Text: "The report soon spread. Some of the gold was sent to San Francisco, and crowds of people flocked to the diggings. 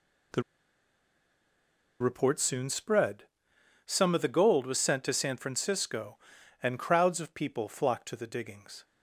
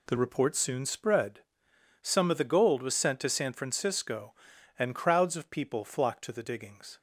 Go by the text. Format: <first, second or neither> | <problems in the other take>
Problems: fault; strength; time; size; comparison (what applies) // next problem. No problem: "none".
second | pauses between "The" and "report"; strong; at 0.4 s; 1.5 s long